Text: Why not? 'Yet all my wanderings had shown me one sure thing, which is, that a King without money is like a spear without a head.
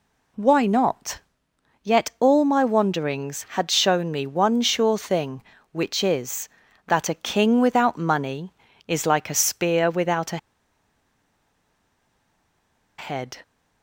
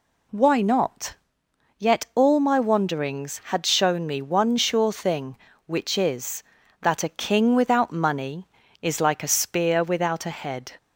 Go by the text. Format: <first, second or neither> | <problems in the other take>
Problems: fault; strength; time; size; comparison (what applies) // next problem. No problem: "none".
second | pauses between "a" and "head"; strong; at 10.3 s; 2.6 s long